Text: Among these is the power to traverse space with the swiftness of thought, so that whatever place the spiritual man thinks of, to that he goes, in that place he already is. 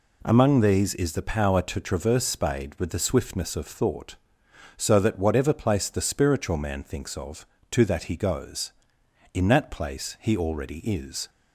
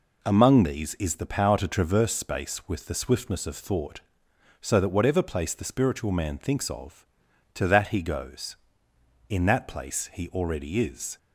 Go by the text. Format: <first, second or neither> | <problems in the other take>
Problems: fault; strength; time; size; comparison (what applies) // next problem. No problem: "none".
second | says "spade" for "space"; at 2.2 s